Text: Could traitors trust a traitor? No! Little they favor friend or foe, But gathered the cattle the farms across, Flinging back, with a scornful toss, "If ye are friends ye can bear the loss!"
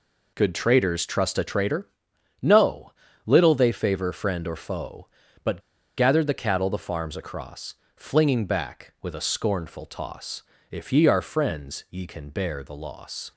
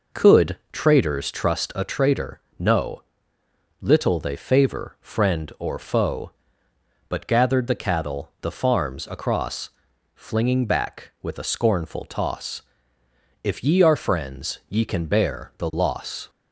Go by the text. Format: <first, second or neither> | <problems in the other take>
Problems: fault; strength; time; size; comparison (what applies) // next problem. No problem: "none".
second | pauses between "But" and "gathered"; at 5.5 s; 0.38 s long